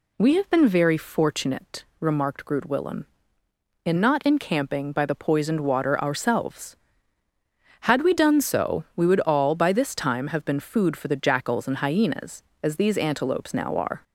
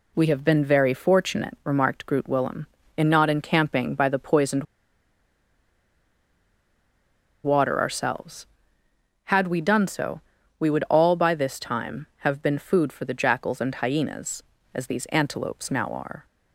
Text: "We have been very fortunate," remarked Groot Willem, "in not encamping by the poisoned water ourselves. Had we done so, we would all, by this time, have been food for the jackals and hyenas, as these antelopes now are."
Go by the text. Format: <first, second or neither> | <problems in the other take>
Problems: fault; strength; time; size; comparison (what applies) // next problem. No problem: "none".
first | pauses between "poisoned" and "water"; strong; at 4.6 s; 2.8 s long